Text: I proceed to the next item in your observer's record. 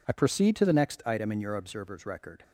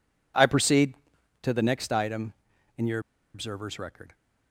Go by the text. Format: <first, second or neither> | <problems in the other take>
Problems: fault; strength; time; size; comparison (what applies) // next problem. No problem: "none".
first | pauses between "your" and "observer's"; slight; at 2.9 s; 0.35 s long